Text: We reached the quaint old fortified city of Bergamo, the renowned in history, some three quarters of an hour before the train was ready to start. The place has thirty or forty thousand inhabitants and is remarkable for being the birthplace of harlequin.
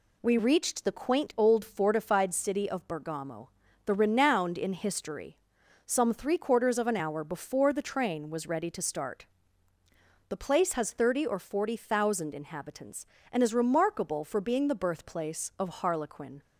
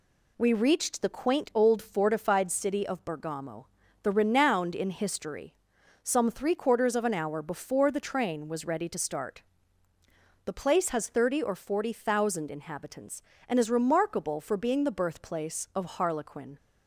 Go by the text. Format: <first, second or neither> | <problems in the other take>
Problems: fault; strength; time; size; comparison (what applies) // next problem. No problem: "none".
neither | none